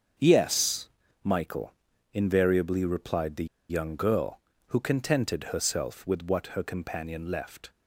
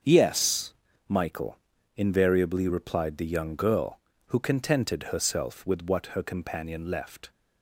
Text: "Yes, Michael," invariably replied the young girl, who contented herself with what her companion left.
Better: second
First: starts louder than the rest; until 1.5 s; 7 dB // pauses between "the" and "young"; slight; at 3.4 s; 0.24 s long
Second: starts louder than the rest; until 1.3 s; 7 dB

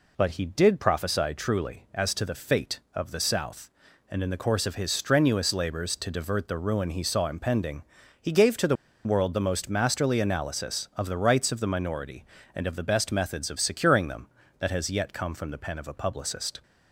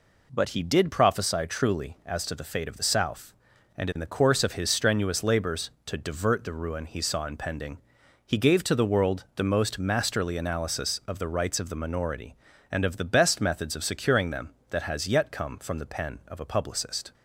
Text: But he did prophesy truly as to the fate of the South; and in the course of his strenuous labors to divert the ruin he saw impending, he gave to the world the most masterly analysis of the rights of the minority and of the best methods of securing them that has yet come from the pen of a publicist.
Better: second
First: pauses between "the" and "world"; slight; at 8.7 s; 0.30 s long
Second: none

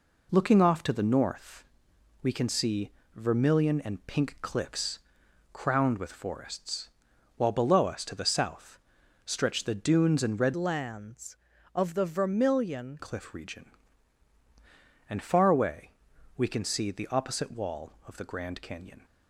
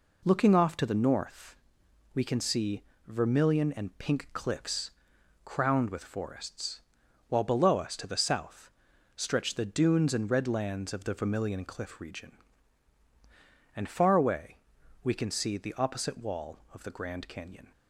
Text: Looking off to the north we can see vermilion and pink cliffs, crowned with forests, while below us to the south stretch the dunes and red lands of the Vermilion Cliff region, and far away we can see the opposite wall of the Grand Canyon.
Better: second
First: pauses between "north" and "we"; noticeable; at 1.6 s; 0.58 s long // pauses between "see" and "vermilion"; slight; at 2.9 s; 0.26 s long // pauses between "south" and "stretch"; noticeable; at 8.7 s; 0.46 s long // changes voice from "lands" to "Vermilion"; from 10.5 to 12.9 s; 2.4 s long // pauses between "away" and "we"; noticeable; at 15.9 s; 0.46 s long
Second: pauses between "north" and "we"; noticeable; at 1.5 s; 0.58 s long // pauses between "see" and "vermilion"; slight; at 2.8 s; 0.26 s long // pauses between "south" and "stretch"; at 8.7 s; 0.44 s long // pauses between "away" and "we"; noticeable; at 14.5 s; 0.46 s long

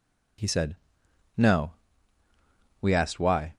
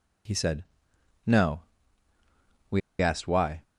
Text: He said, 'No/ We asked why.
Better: first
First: none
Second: pauses between "We" and "asked"; slight; at 2.8 s; 0.20 s long

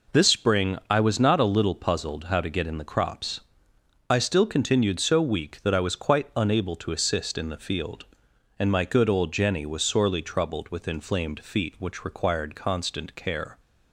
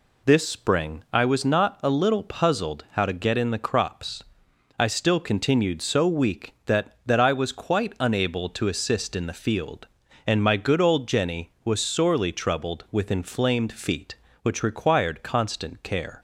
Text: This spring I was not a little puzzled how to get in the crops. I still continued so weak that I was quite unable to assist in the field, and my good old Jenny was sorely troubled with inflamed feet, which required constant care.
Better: first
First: none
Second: says "that" twice; at 7.0 s

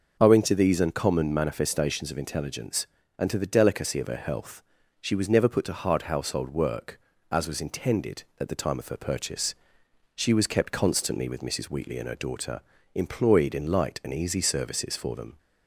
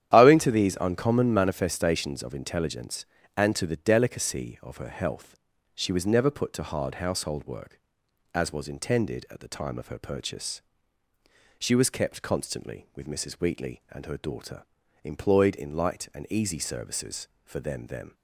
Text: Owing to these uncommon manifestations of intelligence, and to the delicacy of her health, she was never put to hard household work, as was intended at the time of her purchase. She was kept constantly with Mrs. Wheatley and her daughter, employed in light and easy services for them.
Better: first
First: none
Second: starts louder than the rest; strong; until 1.1 s; 10 dB // says "them" twice; at 17.8 s

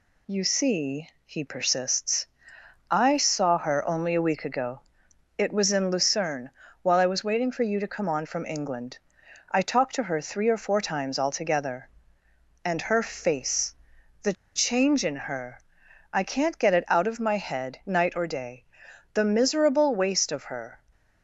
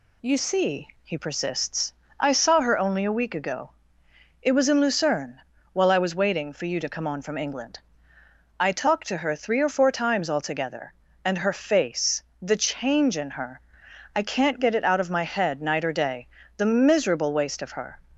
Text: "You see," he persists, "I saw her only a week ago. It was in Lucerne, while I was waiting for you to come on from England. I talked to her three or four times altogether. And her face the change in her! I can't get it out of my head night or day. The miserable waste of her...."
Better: second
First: pauses between "face" and "the"; noticeable; at 13.7 s; 0.48 s long // pauses between "the" and "change"; slight; at 14.3 s; 0.22 s long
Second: pauses between "face" and "the"; slight; at 12.2 s; 0.20 s long

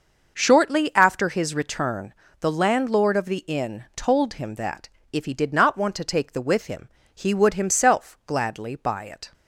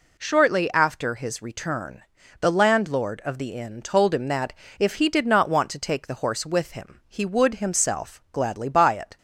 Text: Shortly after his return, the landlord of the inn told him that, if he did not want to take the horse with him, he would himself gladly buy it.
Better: second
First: starts louder than the rest; noticeable; until 1.3 s; 6 dB // skips "horse"; at 6.4 s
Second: none

